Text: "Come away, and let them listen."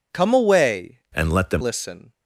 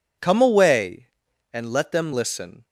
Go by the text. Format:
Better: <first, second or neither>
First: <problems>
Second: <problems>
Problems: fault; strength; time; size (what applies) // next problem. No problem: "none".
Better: second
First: changes voice from "and" to "them"; from 1.1 to 1.6 s; 0.5 s long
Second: none